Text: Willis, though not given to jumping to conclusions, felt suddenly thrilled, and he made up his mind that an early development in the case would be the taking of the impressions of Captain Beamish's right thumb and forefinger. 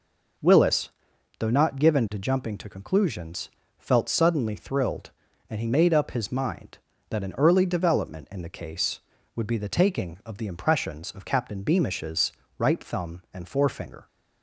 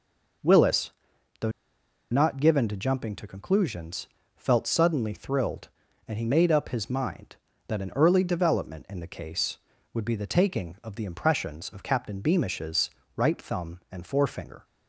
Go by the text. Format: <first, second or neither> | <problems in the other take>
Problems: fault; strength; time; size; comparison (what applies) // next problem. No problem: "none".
first | pauses between "though" and "not"; noticeable; at 1.5 s; 0.60 s long // pauses between "Beamish's" and "right"; slight; at 12.9 s; 0.24 s long; slight in the first